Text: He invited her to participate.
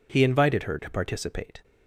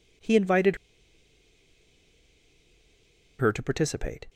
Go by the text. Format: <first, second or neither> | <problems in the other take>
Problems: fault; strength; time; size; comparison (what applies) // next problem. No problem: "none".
first | pauses between "invited" and "her"; strong; at 0.7 s; 2.6 s long